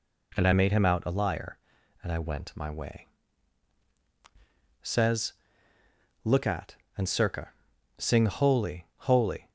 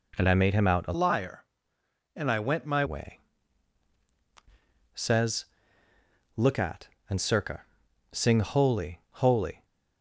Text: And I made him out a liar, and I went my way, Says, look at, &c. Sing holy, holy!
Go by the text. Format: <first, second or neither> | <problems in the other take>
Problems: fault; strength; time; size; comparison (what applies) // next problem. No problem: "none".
first | changes voice from "liar" to "my"; from 0.9 to 2.8 s; 1.9 s long